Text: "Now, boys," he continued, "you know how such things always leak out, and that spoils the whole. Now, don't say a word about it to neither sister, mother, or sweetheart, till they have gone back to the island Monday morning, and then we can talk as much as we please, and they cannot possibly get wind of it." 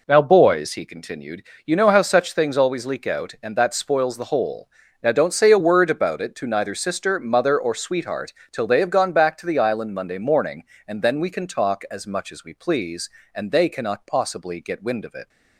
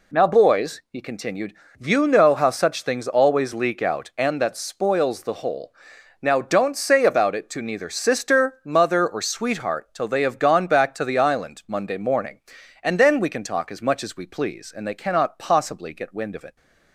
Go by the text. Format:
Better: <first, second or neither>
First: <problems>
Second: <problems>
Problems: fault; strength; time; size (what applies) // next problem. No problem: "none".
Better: first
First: none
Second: skips "a word"; at 7.0 s